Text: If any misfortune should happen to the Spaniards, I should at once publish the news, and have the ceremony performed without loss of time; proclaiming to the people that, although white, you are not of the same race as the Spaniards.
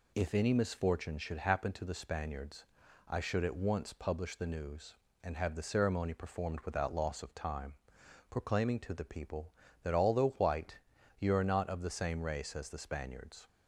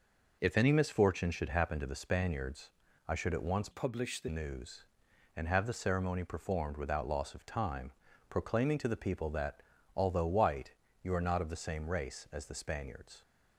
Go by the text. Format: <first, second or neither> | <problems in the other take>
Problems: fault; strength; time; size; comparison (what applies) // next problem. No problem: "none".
first | changes voice from "publish" to "the"; from 3.7 to 4.2 s; 0.5 s long